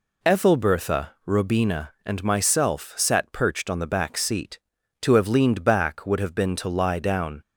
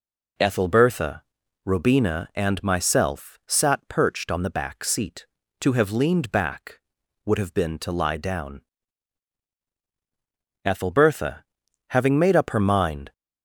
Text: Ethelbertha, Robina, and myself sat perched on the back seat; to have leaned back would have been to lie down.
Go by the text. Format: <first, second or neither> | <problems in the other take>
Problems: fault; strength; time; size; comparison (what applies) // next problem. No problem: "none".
first | goes on to say "Ethelbertha having made up her mind"; strong; from 10.6 s on; 2.4 s long